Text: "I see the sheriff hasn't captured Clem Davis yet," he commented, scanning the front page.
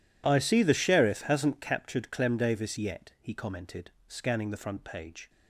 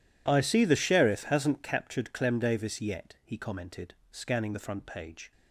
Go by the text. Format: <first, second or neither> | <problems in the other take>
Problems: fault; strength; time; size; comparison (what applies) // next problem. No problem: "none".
neither | none